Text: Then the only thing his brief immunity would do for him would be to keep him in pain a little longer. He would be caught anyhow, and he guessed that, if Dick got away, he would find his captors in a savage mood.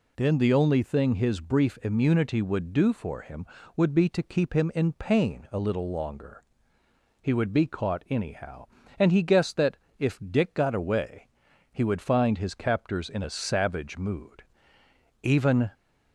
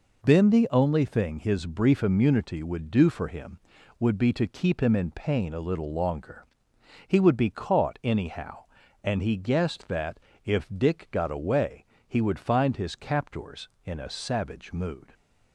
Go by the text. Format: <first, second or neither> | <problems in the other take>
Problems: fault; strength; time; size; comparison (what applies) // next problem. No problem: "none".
second | goes on to say "Even"; slight; from 15.2 s on; 0.48 s long